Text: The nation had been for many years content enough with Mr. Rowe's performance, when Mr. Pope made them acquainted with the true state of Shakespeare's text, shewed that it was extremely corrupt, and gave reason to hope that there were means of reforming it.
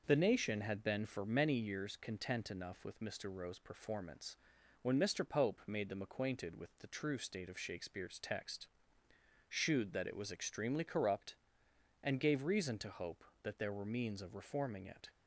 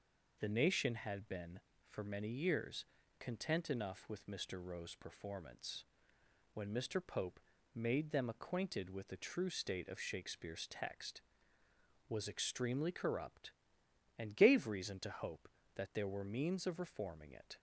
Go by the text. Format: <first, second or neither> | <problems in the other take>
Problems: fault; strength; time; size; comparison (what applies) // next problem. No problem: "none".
first | pauses between "years" and "content"; slight; at 2.8 s; 0.34 s long // pauses between "Pope" and "made"; slight; at 7.3 s; 0.34 s long // skips "shewed that it"; at 11.6 s